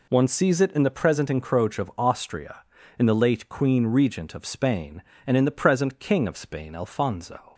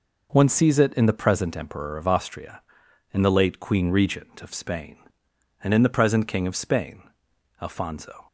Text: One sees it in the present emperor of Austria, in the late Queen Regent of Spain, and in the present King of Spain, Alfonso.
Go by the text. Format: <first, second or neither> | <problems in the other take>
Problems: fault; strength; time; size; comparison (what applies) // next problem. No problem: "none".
second | says "encroach" for "emperor"; at 1.2 s